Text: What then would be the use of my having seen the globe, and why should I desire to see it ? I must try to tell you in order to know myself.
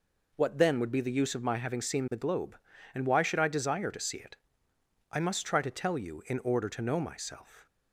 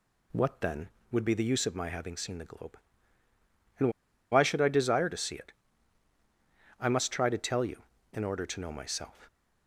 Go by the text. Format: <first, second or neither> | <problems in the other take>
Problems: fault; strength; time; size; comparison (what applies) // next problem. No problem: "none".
first | pauses between "and" and "why"; at 3.8 s; 0.42 s long